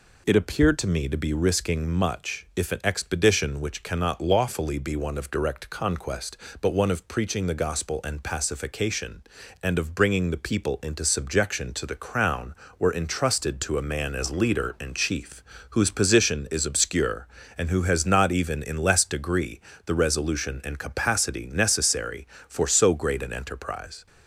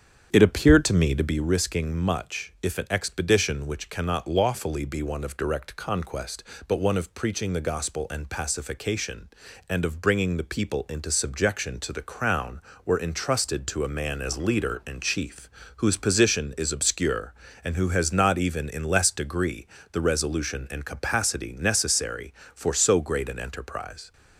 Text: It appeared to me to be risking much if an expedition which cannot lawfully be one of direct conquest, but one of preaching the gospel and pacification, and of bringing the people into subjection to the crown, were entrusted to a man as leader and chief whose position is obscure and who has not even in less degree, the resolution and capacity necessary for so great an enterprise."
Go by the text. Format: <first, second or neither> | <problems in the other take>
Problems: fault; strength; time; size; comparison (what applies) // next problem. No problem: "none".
first | starts louder than the rest; strong; until 1.4 s; 8 dB // pauses between "chief" and "whose"; slight; at 15.4 s; 0.28 s long; slight in the first